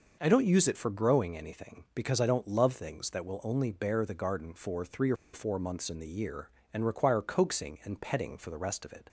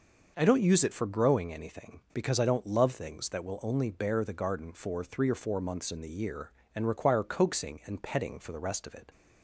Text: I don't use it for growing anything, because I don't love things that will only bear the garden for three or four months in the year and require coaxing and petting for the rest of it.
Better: second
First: pauses between "or" and "four"; slight; at 5.1 s; 0.18 s long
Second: none

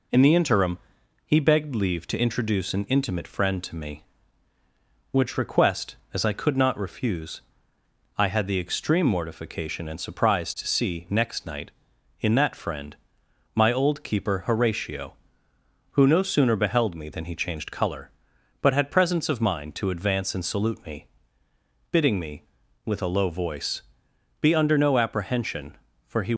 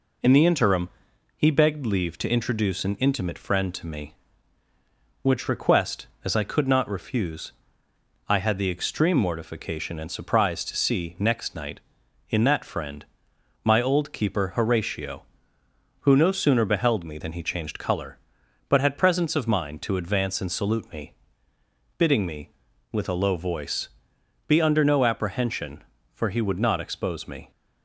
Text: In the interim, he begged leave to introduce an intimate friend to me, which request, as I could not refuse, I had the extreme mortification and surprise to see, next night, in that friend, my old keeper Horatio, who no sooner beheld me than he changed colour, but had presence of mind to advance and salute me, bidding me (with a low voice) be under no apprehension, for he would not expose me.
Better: second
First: stops before "would not expose me"; at 26.3 s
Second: none

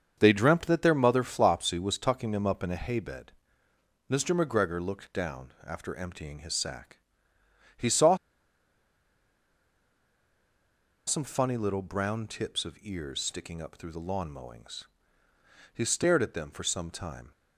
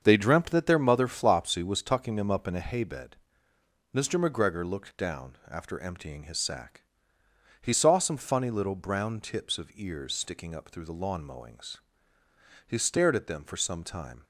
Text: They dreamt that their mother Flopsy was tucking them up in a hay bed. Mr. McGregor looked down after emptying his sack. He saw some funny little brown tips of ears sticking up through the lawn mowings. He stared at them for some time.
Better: second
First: starts louder than the rest; until 1.1 s; 7 dB // pauses between "saw" and "some"; strong; at 8.1 s; 2.9 s long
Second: starts louder than the rest; until 1.0 s; 7 dB

